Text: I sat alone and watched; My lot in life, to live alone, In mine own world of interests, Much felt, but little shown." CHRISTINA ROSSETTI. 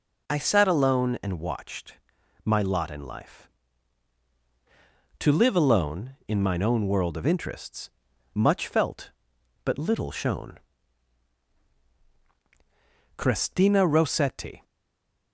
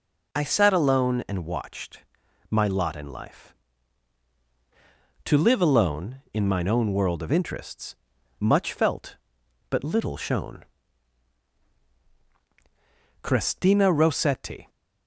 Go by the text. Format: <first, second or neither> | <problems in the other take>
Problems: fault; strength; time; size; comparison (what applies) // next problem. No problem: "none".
second | stays silent after the last word; slight; from 14.6 s on; 0.7 s long